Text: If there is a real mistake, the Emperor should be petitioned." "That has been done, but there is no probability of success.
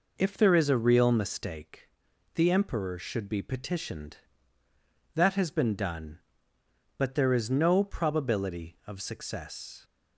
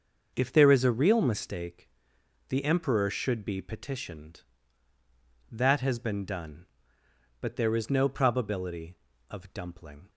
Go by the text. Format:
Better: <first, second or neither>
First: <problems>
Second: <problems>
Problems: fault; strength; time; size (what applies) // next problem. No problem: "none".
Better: first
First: none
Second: starts louder than the rest; until 1.3 s; 6.5 dB // says "dumpling" for "success"; at 9.5 s